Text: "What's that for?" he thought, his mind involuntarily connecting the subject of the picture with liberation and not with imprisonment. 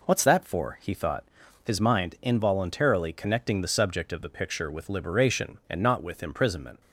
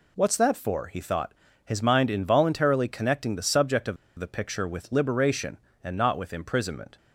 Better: first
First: none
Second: pauses between "of" and "the"; slight; at 3.9 s; 0.22 s long

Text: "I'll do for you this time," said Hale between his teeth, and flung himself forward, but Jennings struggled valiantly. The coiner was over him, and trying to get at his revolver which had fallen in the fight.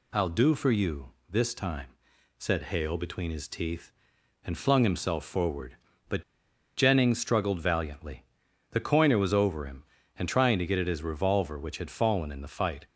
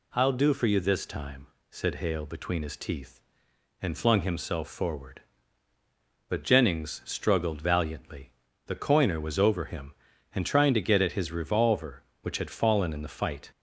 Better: second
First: pauses between "you" and "this"; slight; at 1.1 s; 0.18 s long // pauses between "but" and "Jennings"; noticeable; at 6.2 s; 0.55 s long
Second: none

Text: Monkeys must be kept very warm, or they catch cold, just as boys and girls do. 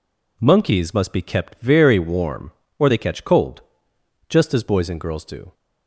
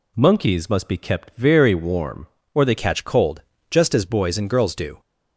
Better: first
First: none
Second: changes voice at "catch"; from 2.7 s on; 2.2 s long

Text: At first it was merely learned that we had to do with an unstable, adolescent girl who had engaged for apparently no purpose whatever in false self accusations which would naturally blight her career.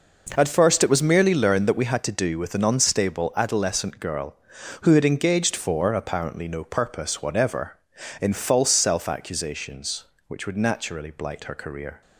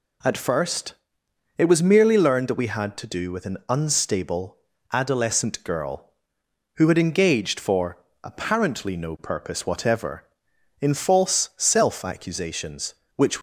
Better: first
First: none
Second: pauses between "first" and "it"; noticeable; at 0.9 s; 0.62 s long // pauses between "for" and "apparently"; slight; at 7.9 s; 0.26 s long // stops before "would naturally blight her career"; at 13.3 s

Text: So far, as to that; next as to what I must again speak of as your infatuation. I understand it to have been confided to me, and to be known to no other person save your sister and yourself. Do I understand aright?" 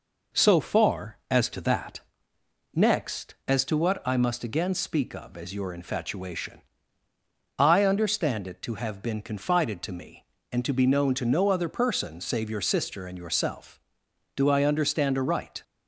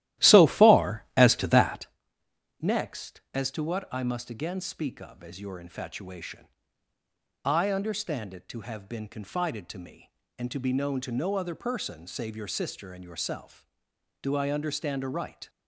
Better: first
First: none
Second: starts louder than the rest; strong; until 1.9 s; 14.5 dB

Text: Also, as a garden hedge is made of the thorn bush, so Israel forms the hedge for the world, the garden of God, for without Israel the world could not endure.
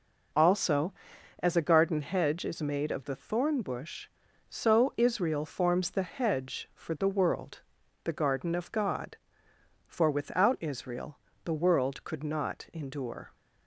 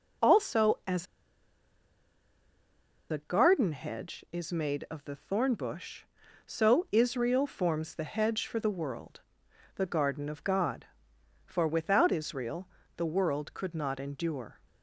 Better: first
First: pauses between "Israel" and "the"; slight; at 11.1 s; 0.26 s long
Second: pauses between "as" and "a"; strong; at 1.0 s; 2.0 s long // pauses between "Israel" and "the"; slight; at 12.6 s; 0.30 s long

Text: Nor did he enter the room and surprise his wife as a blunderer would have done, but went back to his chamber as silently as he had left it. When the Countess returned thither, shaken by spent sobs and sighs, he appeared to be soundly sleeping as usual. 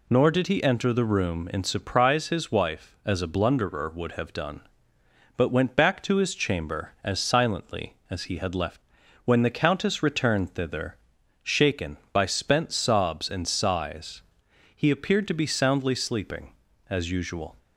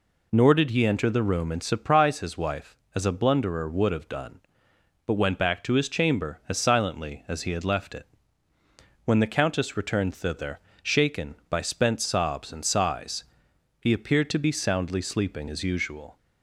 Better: second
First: skips "it"; at 9.0 s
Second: none

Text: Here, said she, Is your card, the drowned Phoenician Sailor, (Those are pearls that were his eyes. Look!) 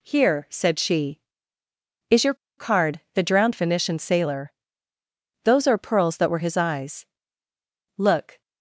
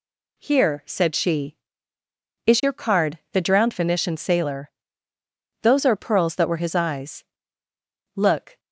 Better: second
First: pauses between "your" and "card"; slight; at 2.3 s; 0.23 s long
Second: none

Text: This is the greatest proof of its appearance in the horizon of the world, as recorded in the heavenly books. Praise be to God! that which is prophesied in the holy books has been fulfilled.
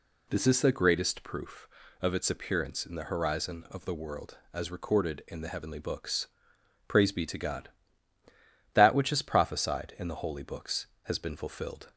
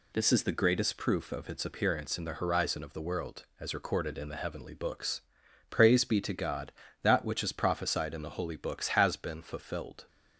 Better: neither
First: none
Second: none

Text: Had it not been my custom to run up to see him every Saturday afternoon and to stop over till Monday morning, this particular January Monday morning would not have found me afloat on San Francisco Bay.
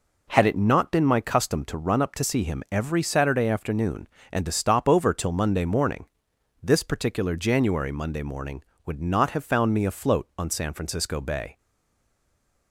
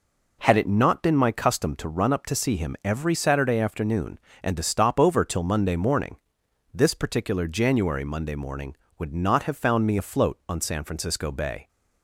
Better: second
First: stays silent after the last word; noticeable; from 11.5 s on; 1.2 s long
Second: none

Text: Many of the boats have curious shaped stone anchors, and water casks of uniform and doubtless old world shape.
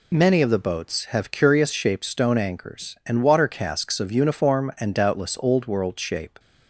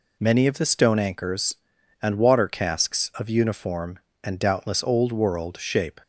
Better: first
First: none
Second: skips "boats have curious shaped"; at 0.6 s

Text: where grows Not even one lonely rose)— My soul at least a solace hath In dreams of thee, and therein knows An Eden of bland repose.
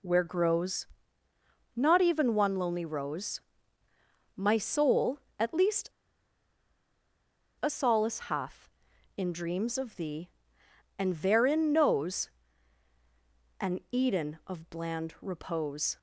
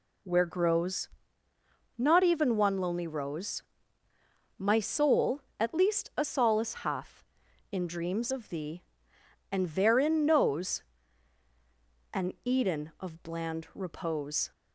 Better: second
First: pauses between "grows" and "Not"; noticeable; at 0.8 s; 0.90 s long // pauses between "least" and "a"; strong; at 5.9 s; 1.7 s long // pauses between "knows" and "An"; strong; at 12.2 s; 1.3 s long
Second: pauses between "grows" and "Not"; noticeable; at 1.0 s; 0.90 s long // pauses between "knows" and "An"; strong; at 10.8 s; 1.3 s long

